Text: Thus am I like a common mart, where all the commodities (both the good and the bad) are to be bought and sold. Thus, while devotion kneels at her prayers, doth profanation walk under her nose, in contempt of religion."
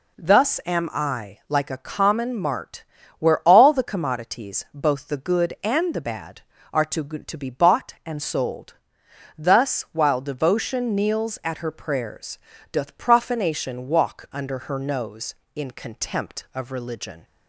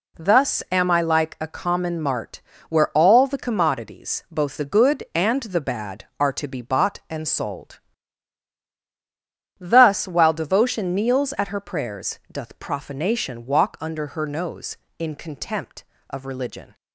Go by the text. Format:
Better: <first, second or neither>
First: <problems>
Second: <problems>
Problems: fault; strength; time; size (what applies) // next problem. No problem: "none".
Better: second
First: says "to" twice; at 7.0 s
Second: none